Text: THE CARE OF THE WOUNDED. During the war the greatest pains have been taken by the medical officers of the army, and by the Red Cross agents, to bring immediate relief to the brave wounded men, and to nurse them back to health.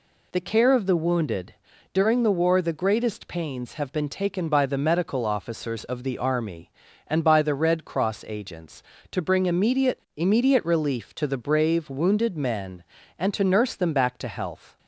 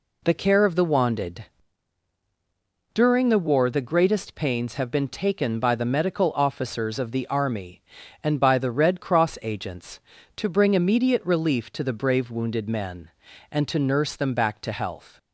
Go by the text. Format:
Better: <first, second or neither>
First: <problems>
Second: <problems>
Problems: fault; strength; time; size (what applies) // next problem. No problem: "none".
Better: second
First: says "immediate" twice; at 10.1 s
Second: none